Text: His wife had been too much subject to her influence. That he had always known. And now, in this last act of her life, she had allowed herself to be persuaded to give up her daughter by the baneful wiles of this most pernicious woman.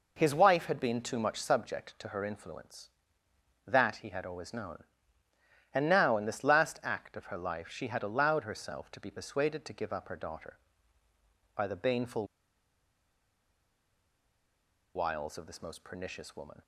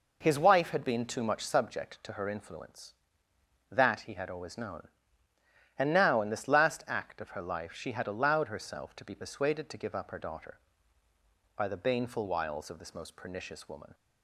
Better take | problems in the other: second | pauses between "baneful" and "wiles"; strong; at 12.2 s; 2.7 s long

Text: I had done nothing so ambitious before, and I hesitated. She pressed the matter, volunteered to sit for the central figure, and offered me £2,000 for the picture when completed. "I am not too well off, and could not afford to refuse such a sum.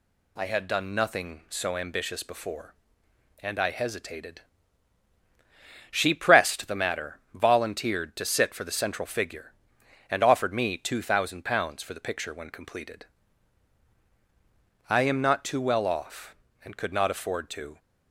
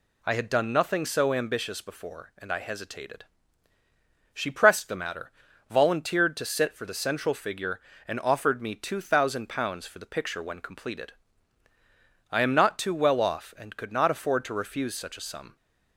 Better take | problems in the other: second | stops before "refuse such a sum"; at 17.7 s

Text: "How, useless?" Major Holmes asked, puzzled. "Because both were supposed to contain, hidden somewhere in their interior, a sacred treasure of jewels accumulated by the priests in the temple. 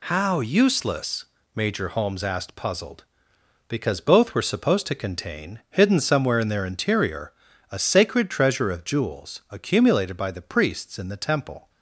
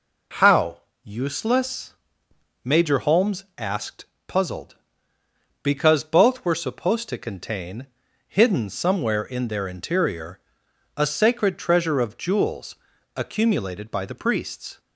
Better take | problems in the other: first | pauses between "jewels" and "accumulated"; at 12.7 s; 0.38 s long // stops before "in the temple"; at 14.7 s

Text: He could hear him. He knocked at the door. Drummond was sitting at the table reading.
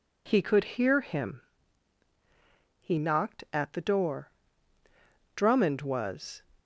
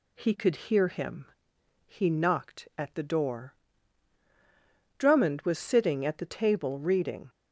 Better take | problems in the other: second | stops before "sitting at the table reading"; at 6.5 s

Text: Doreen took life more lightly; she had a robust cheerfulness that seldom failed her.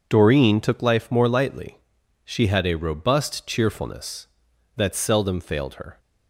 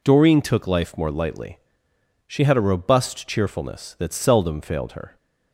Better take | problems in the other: neither | none

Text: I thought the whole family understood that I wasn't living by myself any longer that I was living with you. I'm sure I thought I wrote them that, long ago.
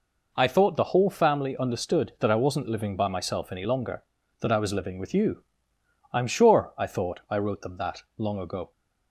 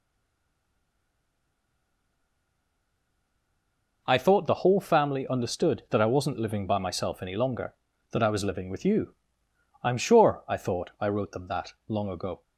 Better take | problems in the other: first | stays silent before the first word; strong; until 4.0 s; 4.0 s long

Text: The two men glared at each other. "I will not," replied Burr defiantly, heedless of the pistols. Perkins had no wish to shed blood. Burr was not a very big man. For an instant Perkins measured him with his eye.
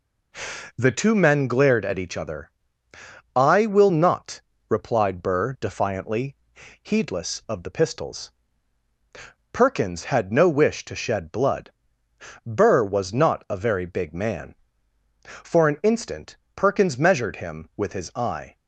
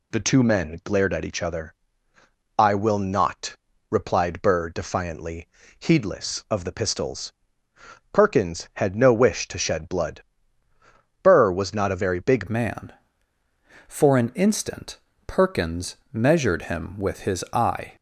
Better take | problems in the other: first | changes voice at "man"; from 12.4 s on; 5.5 s long // pauses between "instant" and "Perkins"; slight; at 14.9 s; 0.26 s long; slight in the first // pauses between "Perkins" and "measured"; slight; at 15.9 s; 0.18 s long

